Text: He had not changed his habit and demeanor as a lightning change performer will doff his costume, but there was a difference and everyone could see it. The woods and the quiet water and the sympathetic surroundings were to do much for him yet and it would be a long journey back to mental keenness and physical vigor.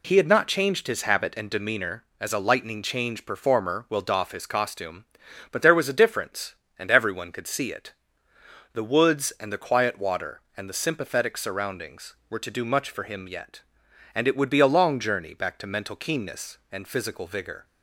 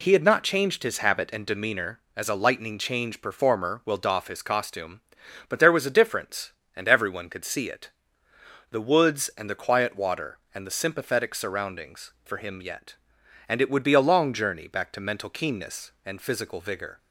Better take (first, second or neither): first